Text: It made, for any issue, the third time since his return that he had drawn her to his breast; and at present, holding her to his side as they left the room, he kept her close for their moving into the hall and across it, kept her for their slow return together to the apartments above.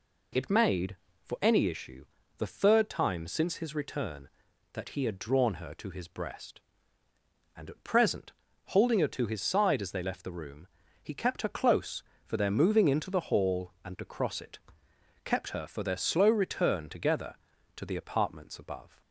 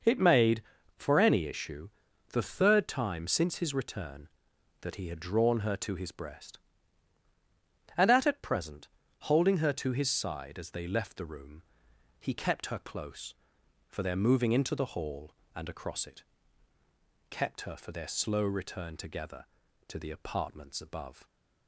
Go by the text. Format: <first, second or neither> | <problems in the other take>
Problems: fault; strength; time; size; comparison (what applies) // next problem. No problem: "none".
first | says "at" twice; at 8.2 s